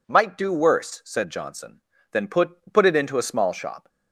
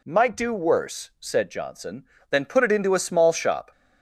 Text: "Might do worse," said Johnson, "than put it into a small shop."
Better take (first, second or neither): second